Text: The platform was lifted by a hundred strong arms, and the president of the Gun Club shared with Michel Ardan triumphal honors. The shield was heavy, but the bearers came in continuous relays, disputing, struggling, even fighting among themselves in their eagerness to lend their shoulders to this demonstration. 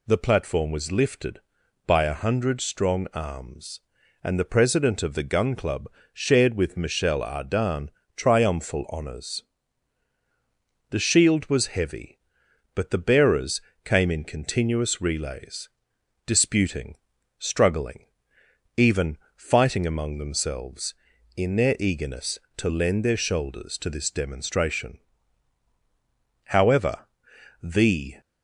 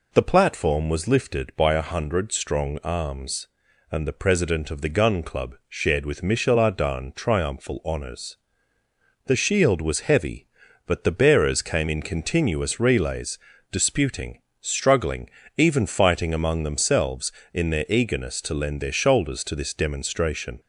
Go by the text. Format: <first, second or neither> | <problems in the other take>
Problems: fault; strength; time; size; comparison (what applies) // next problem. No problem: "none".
second | pauses between "Club" and "shared"; slight; at 5.8 s; 0.26 s long // pauses between "Ardan" and "triumphal"; slight; at 7.8 s; 0.26 s long // pauses between "bearers" and "came"; slight; at 13.6 s; 0.22 s long // pauses between "even" and "fighting"; slight; at 19.1 s; 0.18 s long // goes on to say "However the"; strong; from 26.4 s on; 1.7 s long